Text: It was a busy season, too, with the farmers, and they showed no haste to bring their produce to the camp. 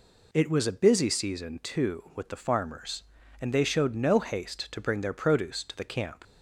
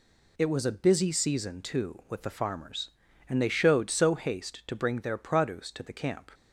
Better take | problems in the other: first | says "so" for "no"; at 3.8 s

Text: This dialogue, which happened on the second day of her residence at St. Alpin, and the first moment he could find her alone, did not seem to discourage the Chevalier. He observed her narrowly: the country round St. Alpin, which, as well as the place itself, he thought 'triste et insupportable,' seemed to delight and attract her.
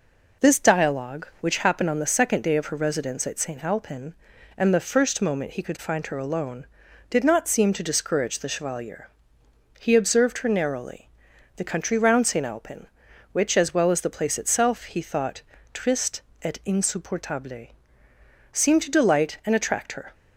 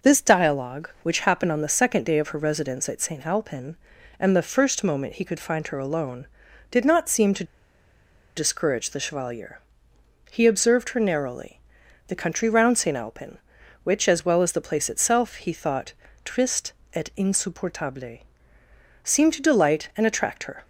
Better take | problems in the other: first | pauses between "to" and "discourage"; noticeable; at 7.4 s; 0.91 s long // pauses between "thought" and "triste"; slight; at 15.9 s; 0.32 s long; slight in the first // pauses between "triste" and "et"; slight; at 16.7 s; 0.20 s long; slight in the first

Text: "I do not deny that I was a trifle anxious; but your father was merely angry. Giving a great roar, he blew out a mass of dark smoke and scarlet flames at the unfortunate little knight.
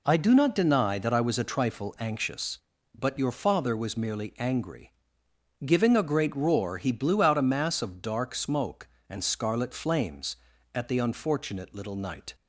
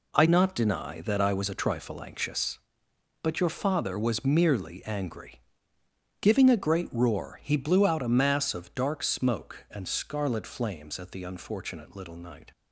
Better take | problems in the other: first | skips "do"; at 0.2 s

